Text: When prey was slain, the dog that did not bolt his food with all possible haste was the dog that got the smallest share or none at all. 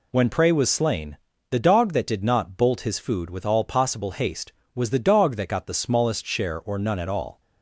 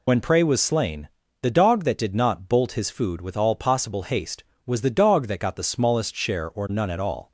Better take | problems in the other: first | loses the start of "When"; at 0.0 s; 40 ms

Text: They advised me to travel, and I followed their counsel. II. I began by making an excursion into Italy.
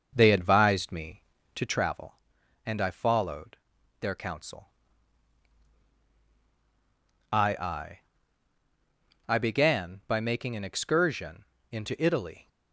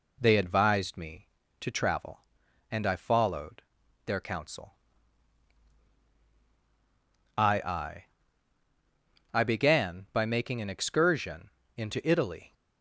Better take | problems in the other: second | starts louder than the rest; noticeable; until 1.9 s; 6 dB // pauses between "followed" and "their"; at 3.5 s; 0.44 s long; also in the second // pauses between "excursion" and "into"; slight; at 11.4 s; 0.28 s long; slight in the second

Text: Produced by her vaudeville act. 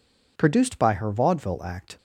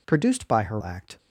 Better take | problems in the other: first | skips "vaudeville"; at 0.8 s

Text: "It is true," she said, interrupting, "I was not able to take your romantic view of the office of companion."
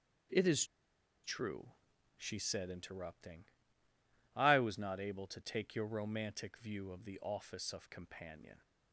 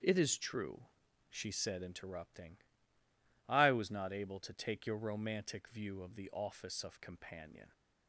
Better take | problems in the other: second | starts louder than the rest; strong; until 2.3 s; 7 dB; strong in the second // pauses between "is" and "true"; noticeable; at 0.6 s; 0.59 s long

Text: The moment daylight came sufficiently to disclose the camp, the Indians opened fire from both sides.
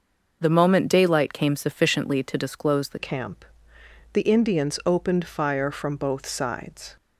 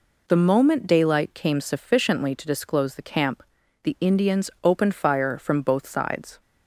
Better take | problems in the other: second | changes voice at "camp"; from 2.9 s on; 4.0 s long

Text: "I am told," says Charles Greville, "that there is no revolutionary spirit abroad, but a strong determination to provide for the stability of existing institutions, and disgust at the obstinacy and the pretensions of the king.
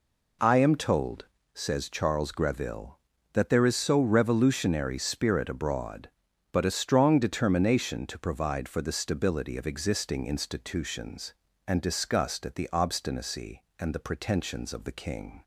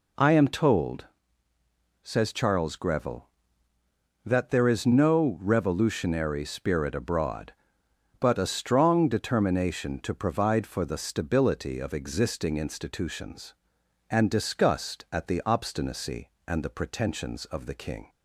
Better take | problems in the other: second | says "so" for "no"; at 3.7 s

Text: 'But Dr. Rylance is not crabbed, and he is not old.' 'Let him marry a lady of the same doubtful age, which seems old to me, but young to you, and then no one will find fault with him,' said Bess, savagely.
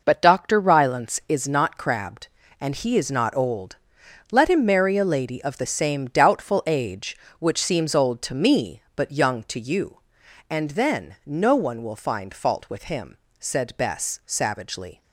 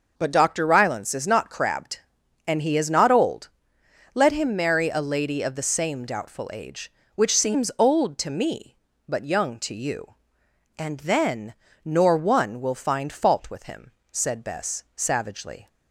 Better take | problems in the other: first | starts louder than the rest; until 1.1 s; 6 dB // says "nor" for "no"; at 11.8 s

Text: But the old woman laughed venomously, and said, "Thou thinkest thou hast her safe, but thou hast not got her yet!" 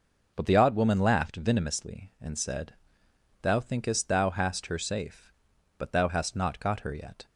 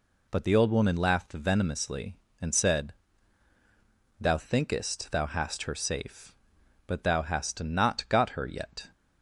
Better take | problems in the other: second | says "odd" for "old"; at 0.5 s

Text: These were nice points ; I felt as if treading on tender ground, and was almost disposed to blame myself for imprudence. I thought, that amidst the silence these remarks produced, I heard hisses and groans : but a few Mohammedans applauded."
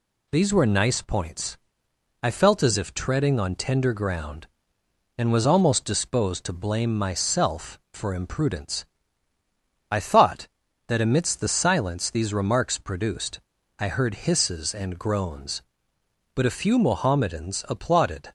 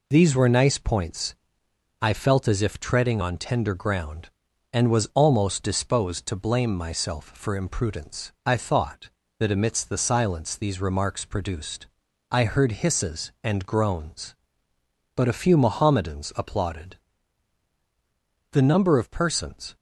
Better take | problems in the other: first | goes on to say "The number of persons"; noticeable; from 18.5 s on; 1.2 s long

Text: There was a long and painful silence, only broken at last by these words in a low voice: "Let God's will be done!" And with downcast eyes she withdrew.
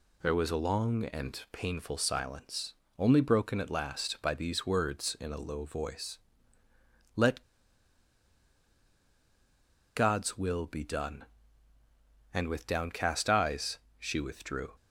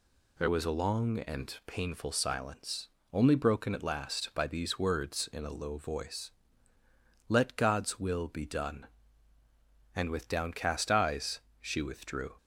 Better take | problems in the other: second | pauses between "Let" and "God's"; strong; at 7.4 s; 2.5 s long // pauses between "eyes" and "she"; slight; at 13.7 s; 0.20 s long; slight in the second

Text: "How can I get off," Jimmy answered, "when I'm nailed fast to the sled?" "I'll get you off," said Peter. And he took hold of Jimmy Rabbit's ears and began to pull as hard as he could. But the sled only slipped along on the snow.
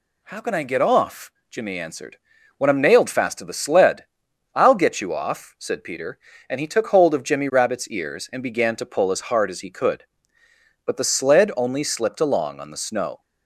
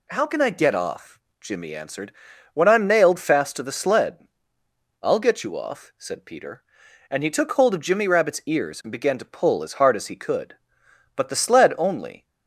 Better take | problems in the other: first | stops before "slipped along on the snow"; at 12.2 s

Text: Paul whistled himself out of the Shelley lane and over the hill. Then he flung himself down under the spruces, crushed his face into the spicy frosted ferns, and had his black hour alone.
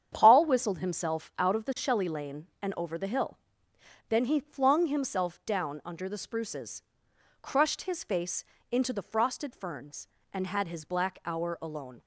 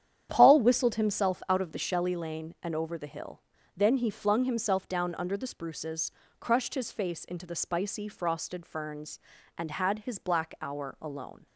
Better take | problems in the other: second | starts louder than the rest; strong; until 1.1 s; 8.5 dB; strong in the second // pauses between "face" and "into"; slight; at 8.4 s; 0.30 s long // skips "spicy"; at 9.0 s

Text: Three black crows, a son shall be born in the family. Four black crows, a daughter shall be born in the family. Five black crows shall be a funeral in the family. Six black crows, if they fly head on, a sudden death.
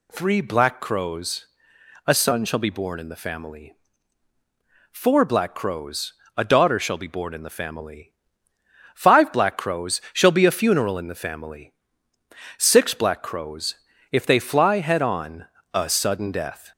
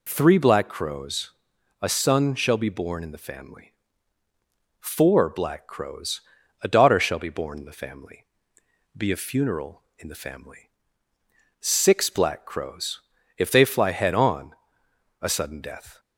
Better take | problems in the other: first | skips "Five black crows shall"; at 8.6 s

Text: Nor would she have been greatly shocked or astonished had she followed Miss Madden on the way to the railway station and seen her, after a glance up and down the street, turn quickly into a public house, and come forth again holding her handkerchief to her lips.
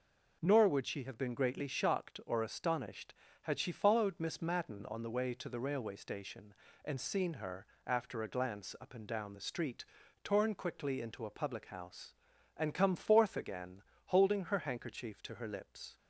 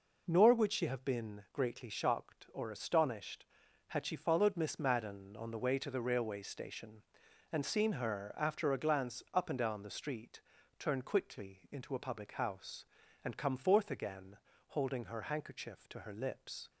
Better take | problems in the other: second | says "torn" for "turn"; at 10.2 s // pauses between "again" and "holding"; slight; at 13.8 s; 0.26 s long; slight in the second

